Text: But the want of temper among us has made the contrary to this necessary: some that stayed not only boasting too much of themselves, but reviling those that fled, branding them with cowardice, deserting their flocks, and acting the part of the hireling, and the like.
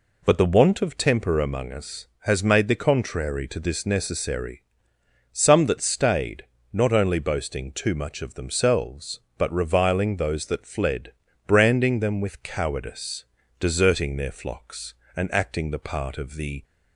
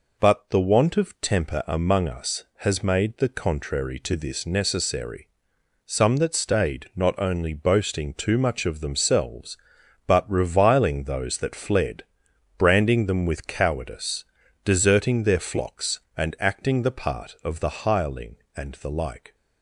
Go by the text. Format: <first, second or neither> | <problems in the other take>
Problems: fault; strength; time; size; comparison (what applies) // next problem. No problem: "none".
second | pauses between "stayed" and "not"; slight; at 6.4 s; 0.26 s long // stops before "hireling and the like"; at 16.6 s